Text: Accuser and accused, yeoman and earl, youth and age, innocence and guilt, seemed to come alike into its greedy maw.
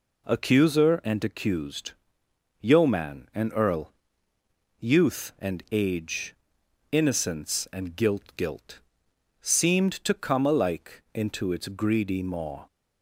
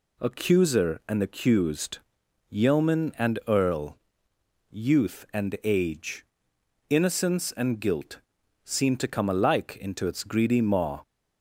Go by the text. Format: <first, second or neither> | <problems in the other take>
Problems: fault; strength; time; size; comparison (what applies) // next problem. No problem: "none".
second | says "guilt" twice; at 8.3 s